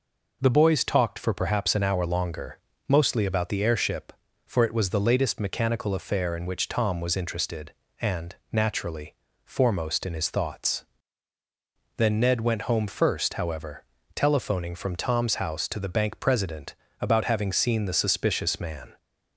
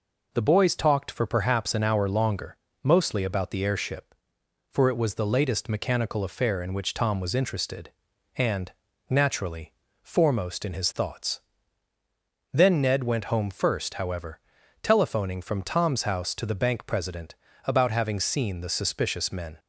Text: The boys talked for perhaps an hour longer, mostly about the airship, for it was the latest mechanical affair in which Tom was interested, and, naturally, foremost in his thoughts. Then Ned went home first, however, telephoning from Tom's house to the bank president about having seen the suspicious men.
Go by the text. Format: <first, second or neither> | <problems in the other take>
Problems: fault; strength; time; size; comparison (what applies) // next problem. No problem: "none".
second | pauses between "president" and "about"; slight; at 16.7 s; 0.26 s long; slight in the second // says "man" for "men"; at 18.5 s